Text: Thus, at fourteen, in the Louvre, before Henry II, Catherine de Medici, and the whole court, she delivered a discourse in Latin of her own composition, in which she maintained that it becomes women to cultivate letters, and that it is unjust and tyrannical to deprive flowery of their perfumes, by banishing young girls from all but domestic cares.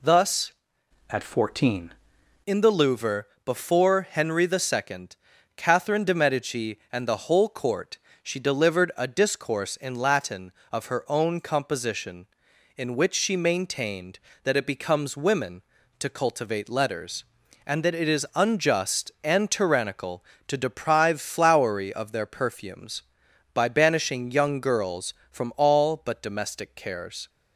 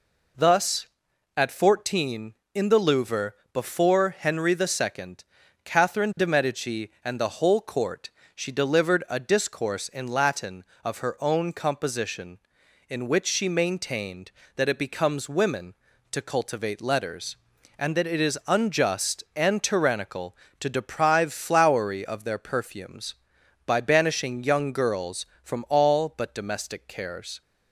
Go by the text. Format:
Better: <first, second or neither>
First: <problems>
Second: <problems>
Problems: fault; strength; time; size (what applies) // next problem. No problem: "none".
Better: second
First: changes voice from "at" to "fourteen"; from 1.0 to 1.9 s; 0.9 s long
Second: none